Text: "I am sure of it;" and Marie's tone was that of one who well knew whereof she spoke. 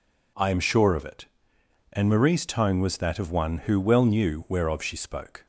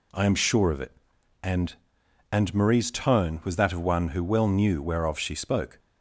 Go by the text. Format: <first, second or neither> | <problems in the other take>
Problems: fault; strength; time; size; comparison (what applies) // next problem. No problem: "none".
first | says "and" twice; at 2.3 s